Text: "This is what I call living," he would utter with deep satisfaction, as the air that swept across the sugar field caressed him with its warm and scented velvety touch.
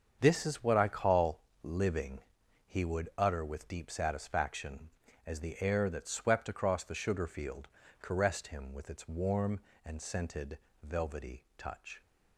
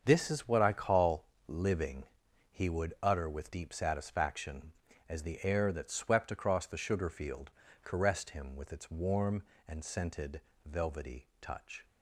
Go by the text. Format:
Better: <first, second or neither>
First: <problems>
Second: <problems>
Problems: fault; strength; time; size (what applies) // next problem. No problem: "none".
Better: neither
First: starts louder than the rest; until 1.2 s; 7 dB // pauses between "call" and "living"; slight; at 1.4 s; 0.20 s long // pauses between "field" and "caressed"; slight; at 7.6 s; 0.32 s long // pauses between "scented" and "velvety"; slight; at 10.5 s; 0.24 s long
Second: starts louder than the rest; until 1.0 s; 7 dB // pauses between "call" and "living"; slight; at 1.2 s; 0.20 s long // pauses between "field" and "caressed"; slight; at 7.5 s; 0.32 s long // pauses between "scented" and "velvety"; slight; at 10.4 s; 0.24 s long